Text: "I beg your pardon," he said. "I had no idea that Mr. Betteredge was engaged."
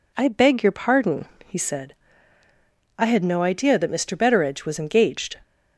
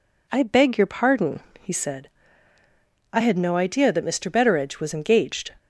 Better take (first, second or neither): neither